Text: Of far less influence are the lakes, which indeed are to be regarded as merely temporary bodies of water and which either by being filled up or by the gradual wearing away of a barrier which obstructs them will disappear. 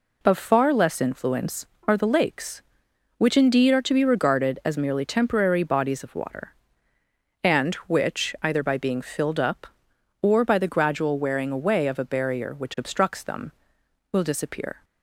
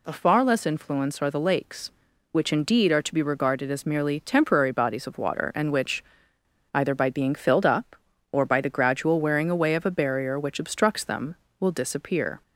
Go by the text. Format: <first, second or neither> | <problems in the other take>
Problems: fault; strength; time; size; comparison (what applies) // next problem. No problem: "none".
first | pauses between "which" and "either"; noticeable; at 6.0 s; 0.69 s long